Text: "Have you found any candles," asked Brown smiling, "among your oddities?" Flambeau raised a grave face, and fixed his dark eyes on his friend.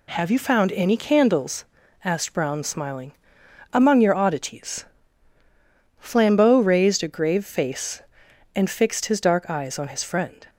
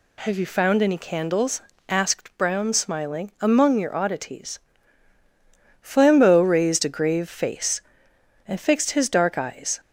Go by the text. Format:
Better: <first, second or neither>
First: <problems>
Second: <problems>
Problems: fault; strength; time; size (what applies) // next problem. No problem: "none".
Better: first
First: none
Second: stops before "on his friend"; at 9.7 s